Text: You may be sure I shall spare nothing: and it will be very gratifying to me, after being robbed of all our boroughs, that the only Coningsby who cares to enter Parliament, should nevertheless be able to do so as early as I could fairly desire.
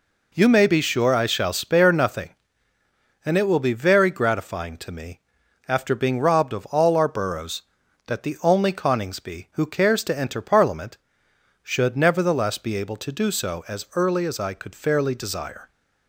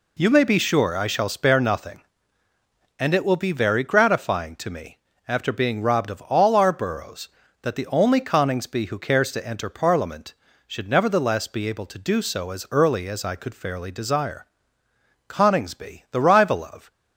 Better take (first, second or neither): first